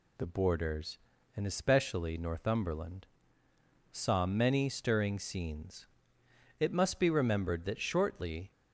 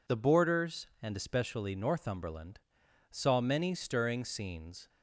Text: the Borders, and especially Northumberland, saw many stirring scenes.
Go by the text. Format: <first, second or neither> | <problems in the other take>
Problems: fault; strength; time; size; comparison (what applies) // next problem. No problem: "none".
second | goes on to say "It must be remembered that shortly"; strong; from 6.6 s on; 1.9 s long